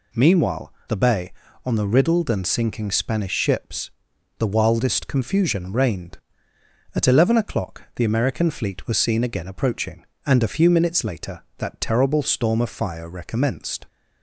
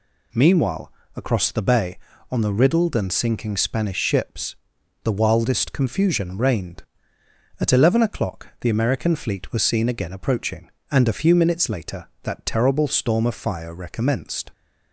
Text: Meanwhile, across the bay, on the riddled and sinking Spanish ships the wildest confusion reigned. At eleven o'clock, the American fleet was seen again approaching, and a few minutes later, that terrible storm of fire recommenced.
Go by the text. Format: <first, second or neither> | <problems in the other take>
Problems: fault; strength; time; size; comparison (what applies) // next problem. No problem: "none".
second | skips "across"; at 0.8 s // pauses between "ships" and "the"; noticeable; at 3.9 s; 0.46 s long; noticeable in the second